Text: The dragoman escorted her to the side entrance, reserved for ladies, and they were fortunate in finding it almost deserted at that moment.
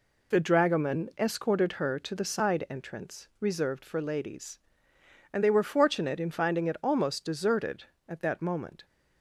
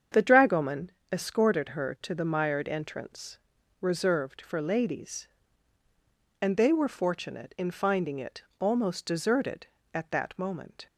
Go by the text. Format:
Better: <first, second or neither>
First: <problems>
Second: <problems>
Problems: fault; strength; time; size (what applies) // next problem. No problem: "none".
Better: first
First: none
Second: starts louder than the rest; strong; until 1.3 s; 7.5 dB // pauses between "dragoman" and "escorted"; slight; at 0.9 s; 0.20 s long // says "mired" for "side"; at 2.2 s // pauses between "it" and "almost"; slight; at 8.4 s; 0.16 s long